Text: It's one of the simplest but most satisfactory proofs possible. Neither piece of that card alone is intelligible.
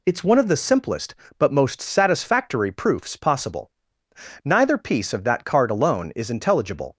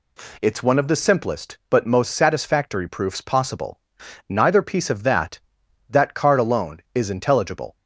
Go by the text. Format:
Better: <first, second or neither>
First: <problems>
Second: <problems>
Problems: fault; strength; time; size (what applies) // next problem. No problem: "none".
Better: first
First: none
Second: says "that" twice; at 5.8 s